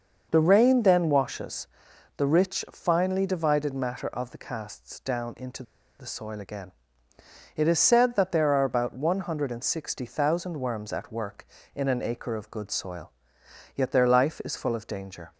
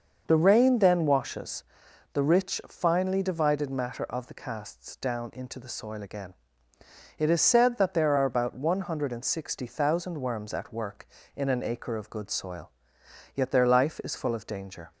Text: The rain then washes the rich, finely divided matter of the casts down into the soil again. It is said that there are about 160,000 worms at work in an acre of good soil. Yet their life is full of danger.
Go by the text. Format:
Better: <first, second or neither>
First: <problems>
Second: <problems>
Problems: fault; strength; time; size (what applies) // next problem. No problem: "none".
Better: second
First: starts louder than the rest; until 1.3 s; 6 dB // pauses between "washes" and "the"; noticeable; at 1.6 s; 0.50 s long // pauses between "into" and "the"; at 5.6 s; 0.36 s long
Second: starts louder than the rest; until 1.2 s; 6.5 dB // pauses between "washes" and "the"; noticeable; at 1.6 s; 0.50 s long